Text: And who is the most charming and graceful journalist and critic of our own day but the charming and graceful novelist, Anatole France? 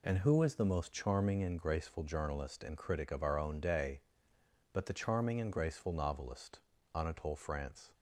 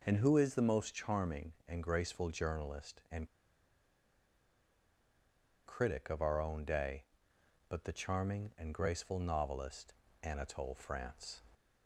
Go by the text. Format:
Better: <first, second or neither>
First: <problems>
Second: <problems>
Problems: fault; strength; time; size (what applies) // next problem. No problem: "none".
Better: first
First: none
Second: pauses between "and" and "critic"; strong; at 3.2 s; 2.3 s long